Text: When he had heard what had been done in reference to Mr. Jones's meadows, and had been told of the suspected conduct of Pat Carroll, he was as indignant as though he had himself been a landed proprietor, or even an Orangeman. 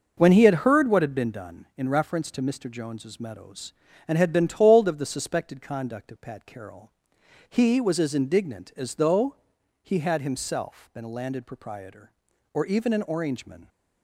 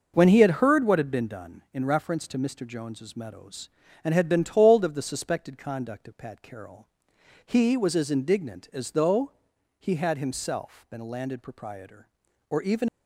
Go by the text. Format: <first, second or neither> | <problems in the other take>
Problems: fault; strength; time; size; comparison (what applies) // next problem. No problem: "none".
first | pauses between "though" and "he"; at 9.3 s; 0.44 s long; also in the first // stops before "an Orangeman"; at 12.8 s